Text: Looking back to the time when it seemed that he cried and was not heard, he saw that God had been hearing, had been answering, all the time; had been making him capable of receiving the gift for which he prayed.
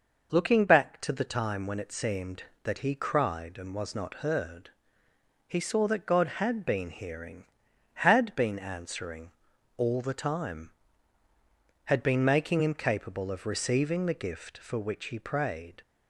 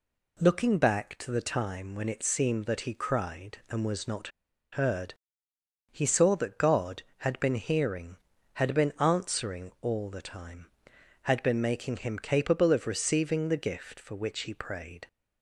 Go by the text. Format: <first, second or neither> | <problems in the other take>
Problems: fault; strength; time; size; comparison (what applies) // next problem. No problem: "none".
first | pauses between "not" and "heard"; at 4.2 s; 0.44 s long